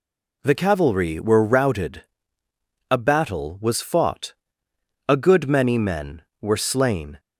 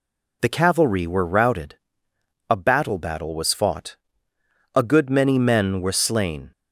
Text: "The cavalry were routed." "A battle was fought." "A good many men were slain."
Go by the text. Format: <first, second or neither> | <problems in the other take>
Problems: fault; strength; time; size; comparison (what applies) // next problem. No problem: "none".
first | says "battle" twice; at 2.9 s